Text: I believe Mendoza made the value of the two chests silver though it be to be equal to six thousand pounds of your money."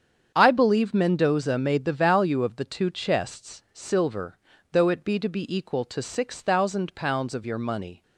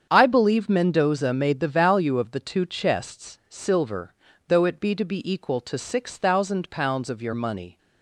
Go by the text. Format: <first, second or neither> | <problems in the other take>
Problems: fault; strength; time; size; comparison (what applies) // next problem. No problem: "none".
neither | starts louder than the rest; strong; the same in both // pauses between "silver" and "though"; slight; the same in both